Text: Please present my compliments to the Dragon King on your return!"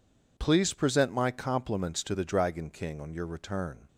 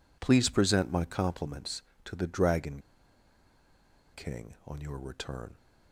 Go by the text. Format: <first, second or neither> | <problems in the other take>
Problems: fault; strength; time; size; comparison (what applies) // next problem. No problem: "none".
first | pauses between "Dragon" and "King"; strong; at 2.8 s; 1.3 s long